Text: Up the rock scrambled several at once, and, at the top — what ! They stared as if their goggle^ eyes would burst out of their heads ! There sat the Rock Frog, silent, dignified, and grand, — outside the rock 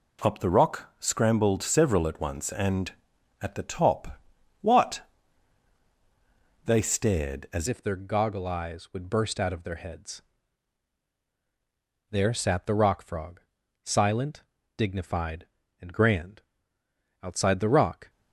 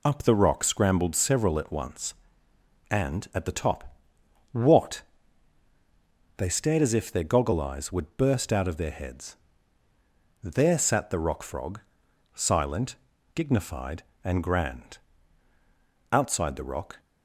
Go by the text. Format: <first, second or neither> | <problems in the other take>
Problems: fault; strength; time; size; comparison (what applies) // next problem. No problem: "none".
second | changes voice at "if"; from 7.6 s on; 10.4 s long